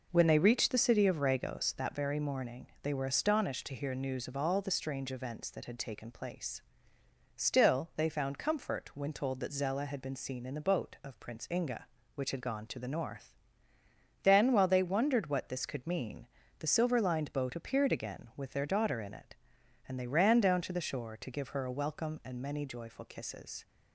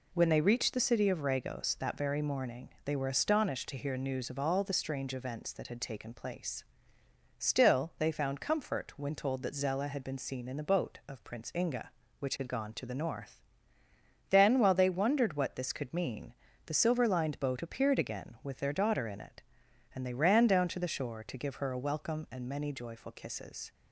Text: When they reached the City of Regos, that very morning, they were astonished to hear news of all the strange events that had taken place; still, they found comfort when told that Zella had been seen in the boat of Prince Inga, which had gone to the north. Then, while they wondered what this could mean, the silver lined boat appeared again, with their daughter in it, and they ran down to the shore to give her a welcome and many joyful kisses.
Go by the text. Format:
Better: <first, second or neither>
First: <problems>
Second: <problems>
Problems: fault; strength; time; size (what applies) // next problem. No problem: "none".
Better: second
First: starts louder than the rest; noticeable; until 1.8 s; 5.5 dB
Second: none